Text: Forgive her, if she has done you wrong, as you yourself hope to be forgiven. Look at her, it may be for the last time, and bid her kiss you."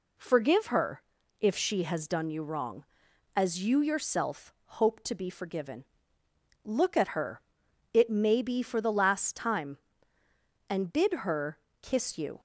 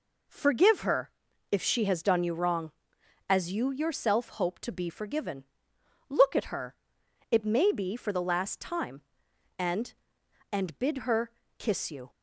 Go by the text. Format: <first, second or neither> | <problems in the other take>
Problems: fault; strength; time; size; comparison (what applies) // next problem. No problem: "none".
first | says "and" twice; at 10.5 s // pauses between "her" and "kiss"; slight; at 11.2 s; 0.28 s long; slight in the first